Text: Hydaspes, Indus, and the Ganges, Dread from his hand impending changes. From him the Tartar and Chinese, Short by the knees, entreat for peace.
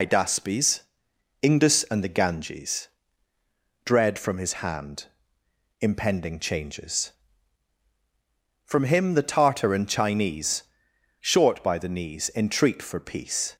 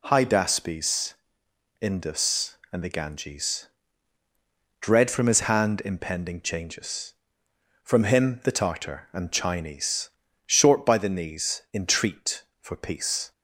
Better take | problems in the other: second | loses the start of "Hydaspes"; at 0.0 s; 60 ms // pauses between "hand" and "impending"; noticeable; at 5.0 s; 0.74 s long

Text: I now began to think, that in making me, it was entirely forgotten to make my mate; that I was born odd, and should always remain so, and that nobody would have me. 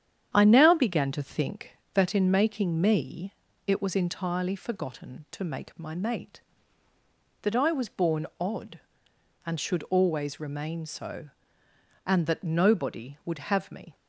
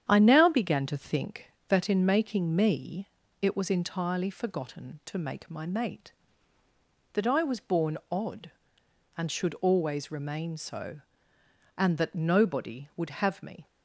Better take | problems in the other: neither | starts louder than the rest; strong; the same in both

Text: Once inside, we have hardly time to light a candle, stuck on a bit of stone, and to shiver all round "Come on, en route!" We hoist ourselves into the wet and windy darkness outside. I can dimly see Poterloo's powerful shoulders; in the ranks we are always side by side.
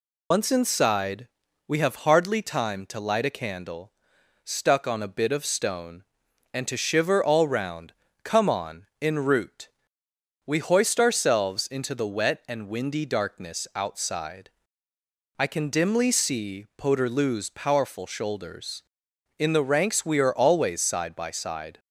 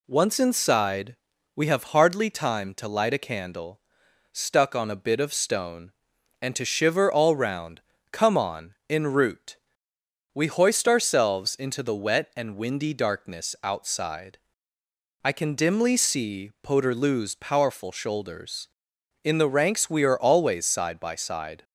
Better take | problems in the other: second | loses the start of "Once"; at 0.3 s; 120 ms // pauses between "round" and "Come"; slight; at 7.9 s; 0.30 s long; slight in the second

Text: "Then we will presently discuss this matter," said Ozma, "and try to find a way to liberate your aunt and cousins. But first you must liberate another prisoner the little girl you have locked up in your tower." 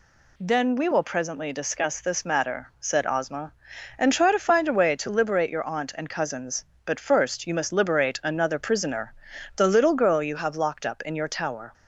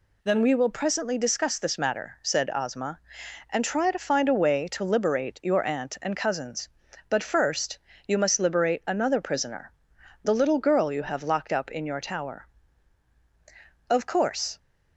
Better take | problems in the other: first | pauses between "first" and "you"; slight; at 7.7 s; 0.28 s long // pauses between "prisoner" and "the"; noticeable; at 9.7 s; 0.50 s long; also in the first // goes on to say "Of course"; noticeable; from 13.8 s on; 0.70 s long

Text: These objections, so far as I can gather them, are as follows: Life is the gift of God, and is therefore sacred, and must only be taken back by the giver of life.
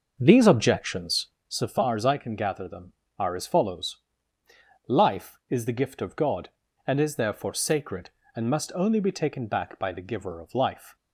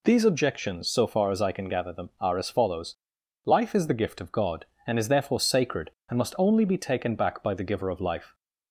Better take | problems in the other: second | starts louder than the rest; noticeable; until 1.4 s; 6 dB

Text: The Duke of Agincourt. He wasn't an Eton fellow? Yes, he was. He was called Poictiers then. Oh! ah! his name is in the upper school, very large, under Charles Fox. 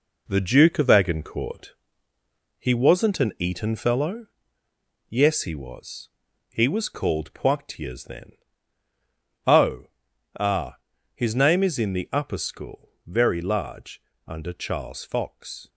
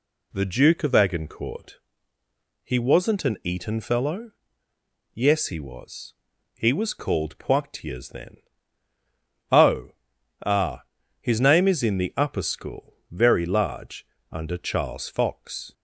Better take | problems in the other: second | gets quieter; throughout; 6.5 dB

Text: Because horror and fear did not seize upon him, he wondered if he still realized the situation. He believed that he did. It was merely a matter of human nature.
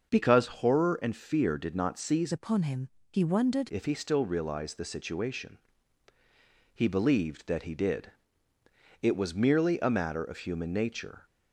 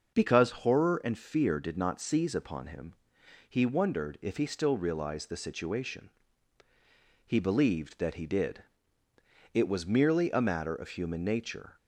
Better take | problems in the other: second | starts louder than the rest; until 1.1 s; 6 dB; noticeable in the second // changes voice from "upon" to "wondered"; from 2.3 to 3.6 s; 1.3 s long

